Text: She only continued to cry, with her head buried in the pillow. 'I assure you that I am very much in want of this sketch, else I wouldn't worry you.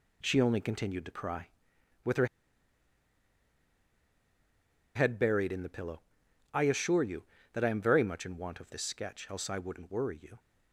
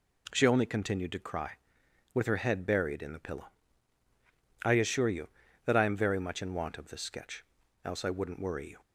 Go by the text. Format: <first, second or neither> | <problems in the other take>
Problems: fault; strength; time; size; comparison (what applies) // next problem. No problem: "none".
second | pauses between "her" and "head"; strong; at 2.2 s; 2.6 s long